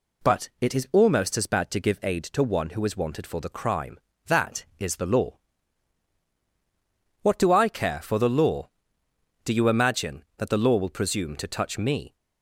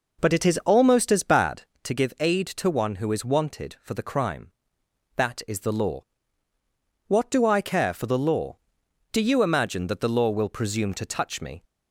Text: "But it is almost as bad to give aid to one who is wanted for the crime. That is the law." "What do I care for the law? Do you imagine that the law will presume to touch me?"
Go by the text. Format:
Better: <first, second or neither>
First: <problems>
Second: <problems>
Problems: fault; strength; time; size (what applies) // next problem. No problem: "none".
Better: first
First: none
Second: starts louder than the rest; noticeable; until 1.9 s; 5 dB